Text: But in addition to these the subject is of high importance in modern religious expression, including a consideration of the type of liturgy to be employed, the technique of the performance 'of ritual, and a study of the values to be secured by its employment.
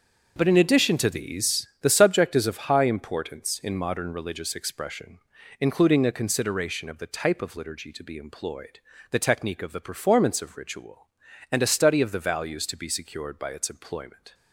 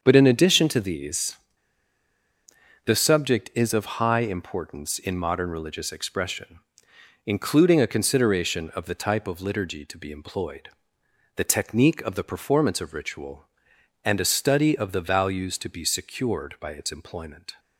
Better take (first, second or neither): first